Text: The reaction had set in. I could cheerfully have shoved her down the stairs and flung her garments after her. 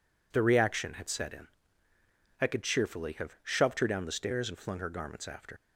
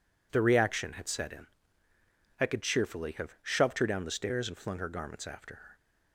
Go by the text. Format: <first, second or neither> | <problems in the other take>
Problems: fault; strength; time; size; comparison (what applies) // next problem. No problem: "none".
second | stops before "her"; at 5.5 s